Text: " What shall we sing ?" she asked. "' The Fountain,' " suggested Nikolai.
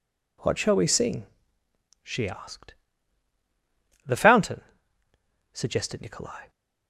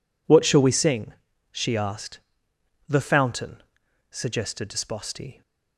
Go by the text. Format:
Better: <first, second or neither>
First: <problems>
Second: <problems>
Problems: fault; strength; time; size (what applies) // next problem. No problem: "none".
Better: first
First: none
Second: says "Disposti" for "Nikolai"; at 4.6 s